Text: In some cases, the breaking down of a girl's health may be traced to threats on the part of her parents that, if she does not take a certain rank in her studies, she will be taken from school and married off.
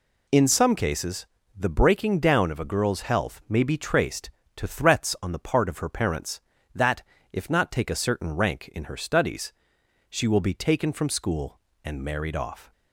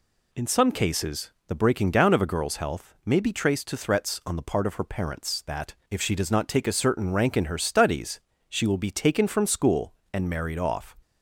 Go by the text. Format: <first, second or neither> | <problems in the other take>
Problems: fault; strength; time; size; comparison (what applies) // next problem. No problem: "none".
second | skips "she does"; at 7.4 s